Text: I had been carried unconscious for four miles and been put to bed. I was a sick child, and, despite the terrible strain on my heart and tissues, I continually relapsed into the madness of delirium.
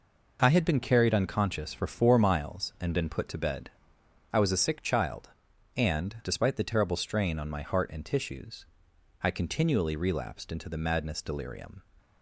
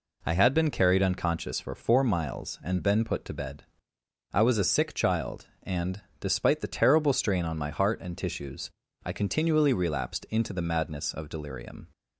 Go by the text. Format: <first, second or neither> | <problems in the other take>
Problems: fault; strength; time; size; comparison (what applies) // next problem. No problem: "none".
second | skips "of"; at 11.2 s